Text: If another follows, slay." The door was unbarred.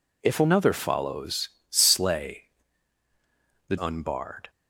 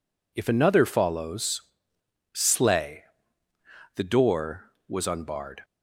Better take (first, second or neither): second